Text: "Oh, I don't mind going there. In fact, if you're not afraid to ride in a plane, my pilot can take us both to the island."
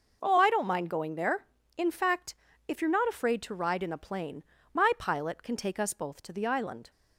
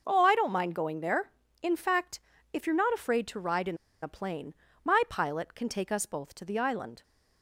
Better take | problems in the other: first | pauses between "in" and "a"; slight; at 3.7 s; 0.25 s long

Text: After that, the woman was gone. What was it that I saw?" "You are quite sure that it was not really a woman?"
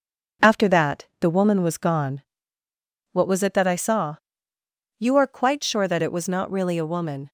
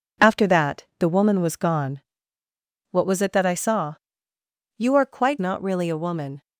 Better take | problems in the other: first | skips "sure that it was"; at 5.4 s

